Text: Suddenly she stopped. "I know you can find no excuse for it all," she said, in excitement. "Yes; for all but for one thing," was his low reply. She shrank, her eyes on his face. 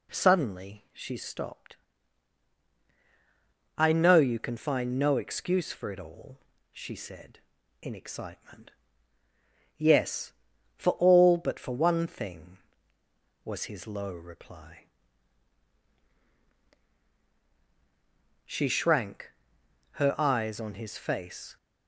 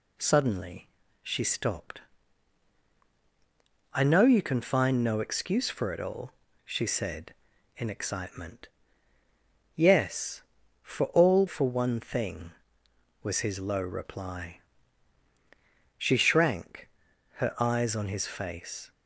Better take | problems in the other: first | pauses between "Suddenly" and "she"; slight; at 0.8 s; 0.34 s long // skips "but"; at 11.4 s

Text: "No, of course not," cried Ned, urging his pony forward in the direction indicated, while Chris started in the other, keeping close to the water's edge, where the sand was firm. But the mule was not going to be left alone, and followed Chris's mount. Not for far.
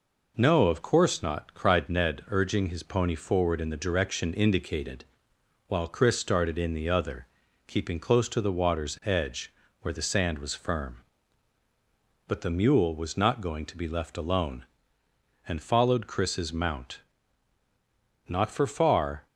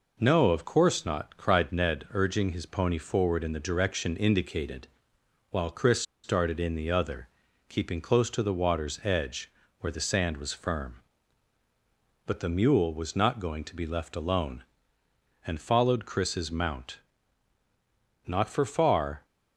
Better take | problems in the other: first | pauses between "Chris" and "started"; slight; at 6.0 s; 0.23 s long

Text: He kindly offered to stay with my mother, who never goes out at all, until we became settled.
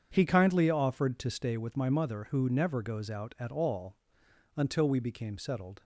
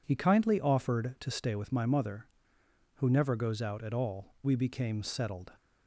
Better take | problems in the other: first | skips "until"; at 4.3 s

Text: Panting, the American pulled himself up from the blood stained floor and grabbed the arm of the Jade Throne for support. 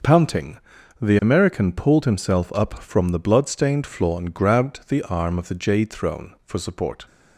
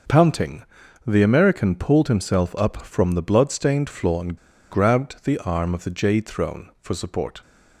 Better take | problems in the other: first | starts louder than the rest; noticeable; until 1.5 s; 6 dB; noticeable in the first // pauses between "and" and "grabbed"; slight; at 4.3 s; 0.35 s long

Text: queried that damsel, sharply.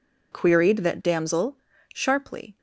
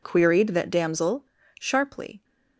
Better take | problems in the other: neither | none

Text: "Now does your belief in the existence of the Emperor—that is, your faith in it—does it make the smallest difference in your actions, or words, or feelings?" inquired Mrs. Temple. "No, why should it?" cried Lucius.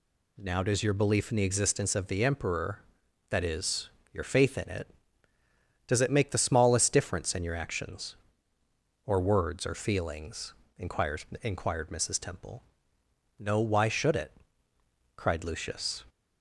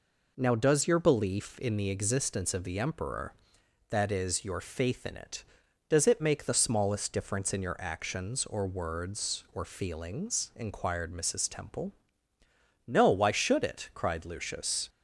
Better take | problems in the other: second | says "inquired" twice; at 11.4 s

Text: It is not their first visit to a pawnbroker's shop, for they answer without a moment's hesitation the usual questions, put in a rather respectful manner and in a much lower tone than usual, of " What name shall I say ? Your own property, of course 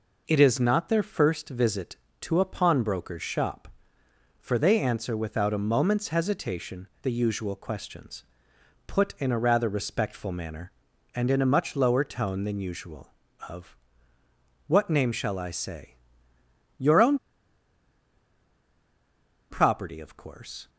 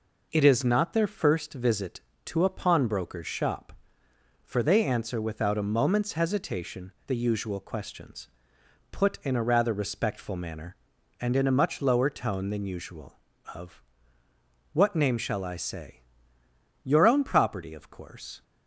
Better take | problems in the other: second | pauses between "own" and "property"; strong; at 17.1 s; 2.3 s long

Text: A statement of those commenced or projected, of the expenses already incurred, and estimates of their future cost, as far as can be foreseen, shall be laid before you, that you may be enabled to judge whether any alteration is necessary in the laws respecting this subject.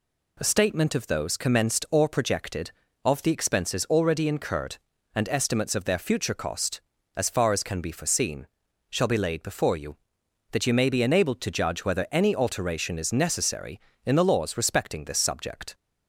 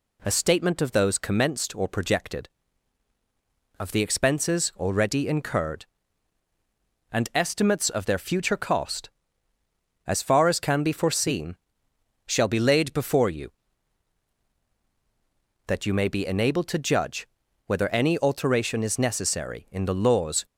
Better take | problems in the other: first | pauses between "judge" and "whether"; at 17.2 s; 0.38 s long // stops before "respecting this subject"; at 20.4 s

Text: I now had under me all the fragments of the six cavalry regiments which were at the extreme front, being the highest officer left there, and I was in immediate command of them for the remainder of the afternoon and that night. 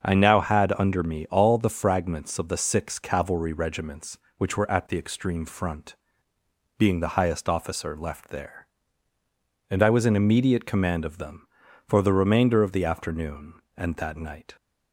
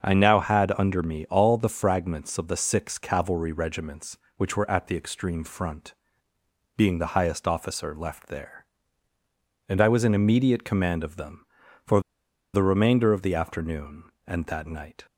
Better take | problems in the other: first | starts louder than the rest; until 1.0 s; 6.5 dB; also in the first // pauses between "for" and "the"; noticeable; at 12.0 s; 0.53 s long

